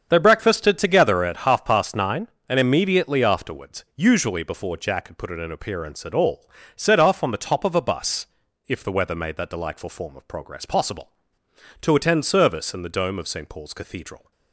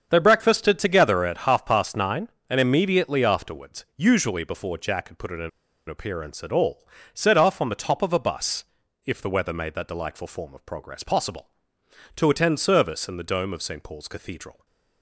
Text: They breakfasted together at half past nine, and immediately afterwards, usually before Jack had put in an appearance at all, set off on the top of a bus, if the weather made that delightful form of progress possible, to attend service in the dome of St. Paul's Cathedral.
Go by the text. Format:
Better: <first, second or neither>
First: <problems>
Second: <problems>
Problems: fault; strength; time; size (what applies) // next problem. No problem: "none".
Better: first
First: starts louder than the rest; strong; until 1.1 s; 7 dB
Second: starts louder than the rest; strong; until 1.1 s; 7 dB // pauses between "an" and "appearance"; at 5.4 s; 0.39 s long